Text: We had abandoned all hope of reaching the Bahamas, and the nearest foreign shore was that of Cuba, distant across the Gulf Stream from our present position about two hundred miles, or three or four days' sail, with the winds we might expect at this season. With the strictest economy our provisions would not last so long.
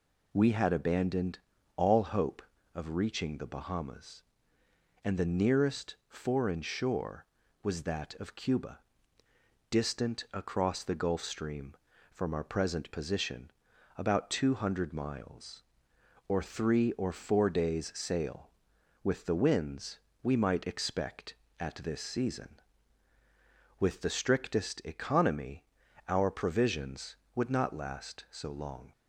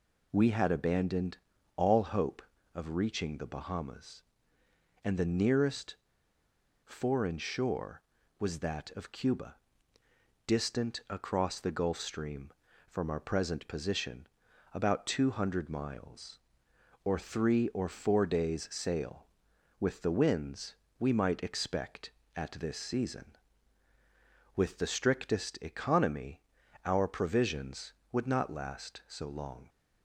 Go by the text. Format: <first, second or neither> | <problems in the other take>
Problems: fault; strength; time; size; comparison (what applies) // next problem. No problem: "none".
first | pauses between "abandoned" and "all"; at 1.3 s; 0.38 s long; also in the first // pauses between "nearest" and "foreign"; noticeable; at 5.9 s; 0.90 s long // pauses between "position" and "about"; noticeable; at 14.2 s; 0.46 s long; noticeable in the first // pauses between "winds" and "we"; slight; at 20.7 s; 0.22 s long; slight in the first // pauses between "economy" and "our"; noticeable; at 26.3 s; 0.46 s long; noticeable in the first